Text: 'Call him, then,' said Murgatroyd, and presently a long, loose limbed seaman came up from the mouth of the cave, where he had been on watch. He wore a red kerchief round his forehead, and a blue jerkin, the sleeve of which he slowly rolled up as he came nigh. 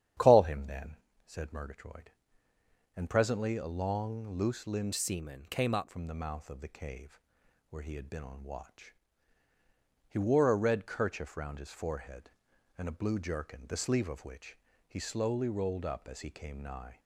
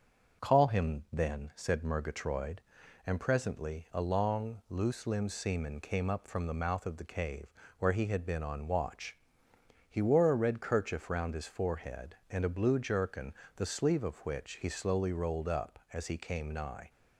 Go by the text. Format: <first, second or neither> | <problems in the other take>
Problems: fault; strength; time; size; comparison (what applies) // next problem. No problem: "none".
second | starts louder than the rest; strong; until 1.4 s; 9.5 dB; also in the second // changes voice from "seaman" to "up"; from 4.9 to 5.8 s; 0.9 s long // pauses between "which" and "he"; slight; at 14.5 s; 0.30 s long